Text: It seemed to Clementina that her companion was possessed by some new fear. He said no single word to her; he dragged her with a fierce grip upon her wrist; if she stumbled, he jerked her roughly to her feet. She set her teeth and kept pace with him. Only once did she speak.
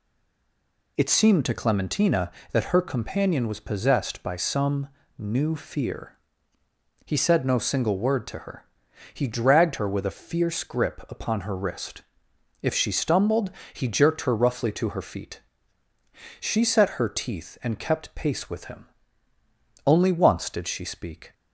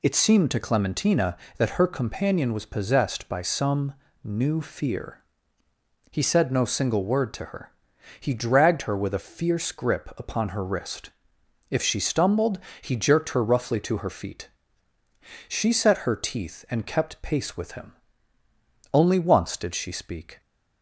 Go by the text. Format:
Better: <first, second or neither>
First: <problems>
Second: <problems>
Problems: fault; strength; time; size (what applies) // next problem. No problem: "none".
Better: second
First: stays silent before the first word; slight; until 0.9 s; 0.9 s long // pauses between "some" and "new"; slight; at 4.8 s; 0.30 s long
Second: pauses between "some" and "new"; slight; at 3.9 s; 0.30 s long